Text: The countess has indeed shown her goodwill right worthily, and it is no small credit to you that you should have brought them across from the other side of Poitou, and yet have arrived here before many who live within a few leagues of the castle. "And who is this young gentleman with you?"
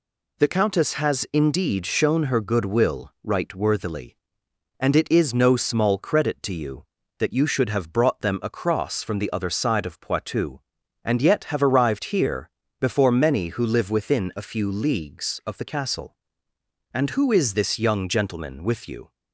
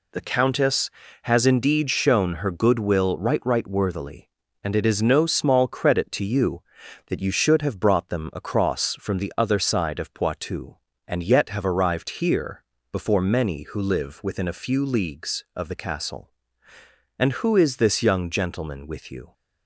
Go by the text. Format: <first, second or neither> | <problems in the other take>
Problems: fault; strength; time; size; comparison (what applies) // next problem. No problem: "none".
first | says "right" twice; at 3.4 s // pauses between "here" and "before"; slight; at 12.6 s; 0.28 s long; slight in the first